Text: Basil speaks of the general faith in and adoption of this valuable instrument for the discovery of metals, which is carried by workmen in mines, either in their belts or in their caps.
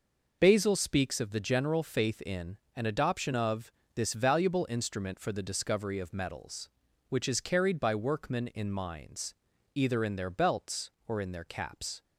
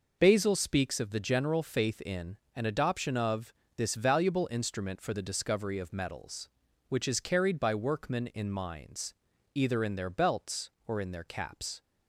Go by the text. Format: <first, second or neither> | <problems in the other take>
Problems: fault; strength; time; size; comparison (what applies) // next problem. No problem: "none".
neither | pauses between "of" and "this"; slight; the same in both